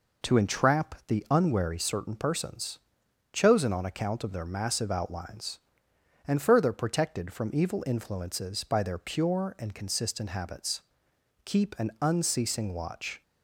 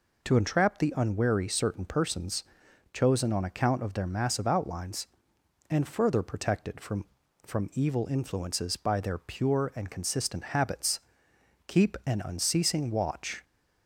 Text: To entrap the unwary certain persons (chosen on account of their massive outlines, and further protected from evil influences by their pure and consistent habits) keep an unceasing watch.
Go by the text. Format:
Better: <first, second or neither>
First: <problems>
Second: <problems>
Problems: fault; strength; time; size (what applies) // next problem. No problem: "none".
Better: first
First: none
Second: says "from" twice; at 7.4 s